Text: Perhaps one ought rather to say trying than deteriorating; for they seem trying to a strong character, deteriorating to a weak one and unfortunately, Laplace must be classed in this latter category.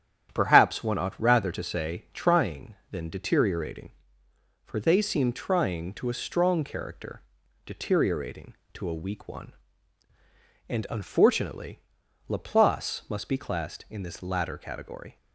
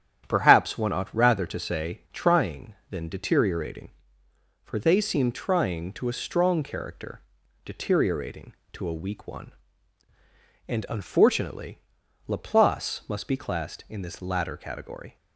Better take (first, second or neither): neither